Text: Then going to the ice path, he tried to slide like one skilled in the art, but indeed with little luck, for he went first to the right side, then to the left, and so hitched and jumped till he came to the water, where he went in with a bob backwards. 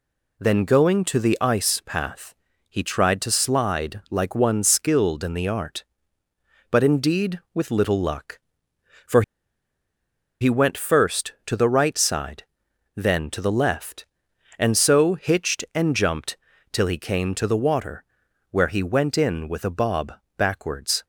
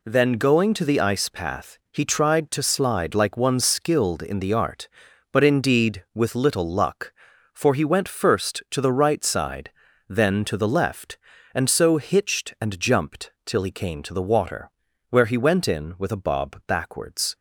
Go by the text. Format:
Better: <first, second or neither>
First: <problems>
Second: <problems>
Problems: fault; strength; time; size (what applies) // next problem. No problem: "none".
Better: second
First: pauses between "for" and "he"; at 9.2 s; 1.1 s long // pauses between "jumped" and "till"; slight; at 16.3 s; 0.36 s long // pauses between "bob" and "backwards"; slight; at 20.1 s; 0.26 s long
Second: pauses between "jumped" and "till"; slight; at 13.3 s; 0.16 s long